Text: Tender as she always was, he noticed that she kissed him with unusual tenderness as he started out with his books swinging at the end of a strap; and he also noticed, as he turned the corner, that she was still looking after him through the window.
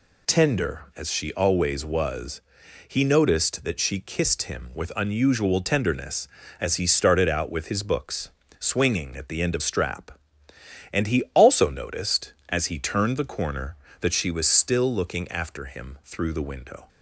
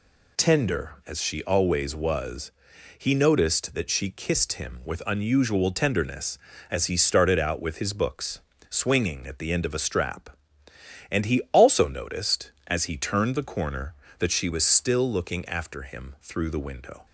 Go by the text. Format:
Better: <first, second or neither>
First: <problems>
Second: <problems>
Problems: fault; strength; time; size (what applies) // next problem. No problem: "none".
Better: second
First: pauses between "books" and "swinging"; slight; at 8.2 s; 0.28 s long // skips "a"; at 9.6 s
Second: pauses between "books" and "swinging"; slight; at 8.4 s; 0.28 s long